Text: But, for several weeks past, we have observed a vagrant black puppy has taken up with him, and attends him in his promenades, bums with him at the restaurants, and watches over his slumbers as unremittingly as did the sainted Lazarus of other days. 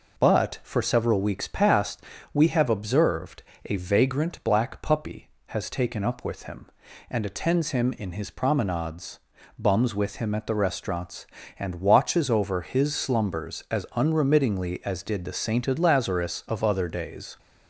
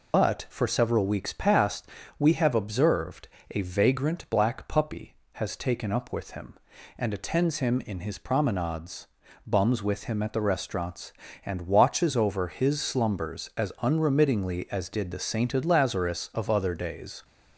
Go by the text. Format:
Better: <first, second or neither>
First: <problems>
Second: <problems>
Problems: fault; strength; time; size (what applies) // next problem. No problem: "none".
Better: first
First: pauses between "observed" and "a"; slight; at 3.4 s; 0.22 s long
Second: loses the start of "But"; at 0.1 s; 85 ms // pauses between "observed" and "a"; slight; at 3.2 s; 0.22 s long